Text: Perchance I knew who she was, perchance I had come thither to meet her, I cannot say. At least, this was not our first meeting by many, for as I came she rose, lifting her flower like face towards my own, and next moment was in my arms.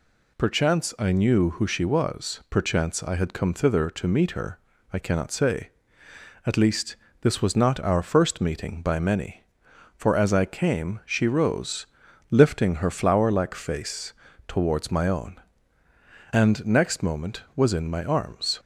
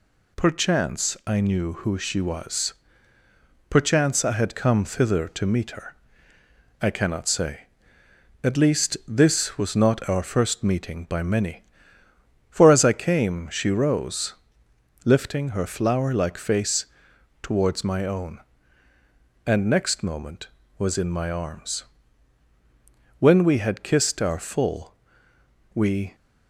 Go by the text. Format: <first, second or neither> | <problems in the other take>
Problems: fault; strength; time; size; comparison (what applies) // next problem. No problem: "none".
first | pauses between "face" and "towards"; noticeable; at 16.8 s; 0.56 s long; slight in the first // goes on to say "When we had kissed our full we"; strong; from 23.1 s on; 2.9 s long